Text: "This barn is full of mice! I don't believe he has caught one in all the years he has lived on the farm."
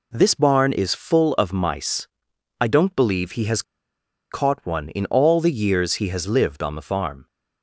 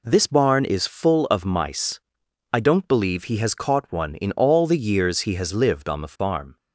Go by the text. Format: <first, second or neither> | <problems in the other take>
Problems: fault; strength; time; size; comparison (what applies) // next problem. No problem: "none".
second | pauses between "has" and "caught"; noticeable; at 3.6 s; 0.69 s long